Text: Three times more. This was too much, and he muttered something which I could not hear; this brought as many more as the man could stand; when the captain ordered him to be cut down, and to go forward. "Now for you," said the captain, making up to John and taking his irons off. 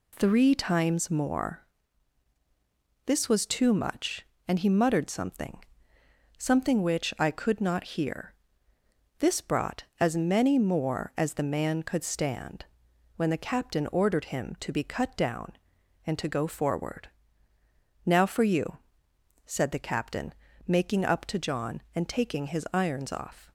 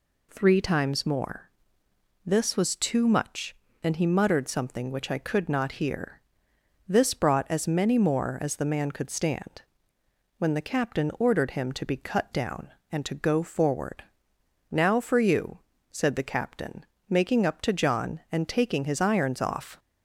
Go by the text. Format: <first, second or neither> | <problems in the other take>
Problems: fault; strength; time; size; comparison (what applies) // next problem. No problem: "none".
second | says "something" twice; at 6.3 s